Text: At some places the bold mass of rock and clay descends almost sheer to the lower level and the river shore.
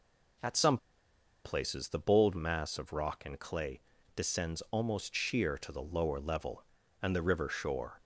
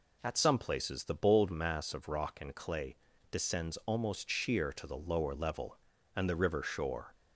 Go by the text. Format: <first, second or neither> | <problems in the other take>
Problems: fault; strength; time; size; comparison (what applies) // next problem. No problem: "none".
second | pauses between "some" and "places"; noticeable; at 0.7 s; 0.66 s long // pauses between "clay" and "descends"; slight; at 3.8 s; 0.34 s long; slight in the second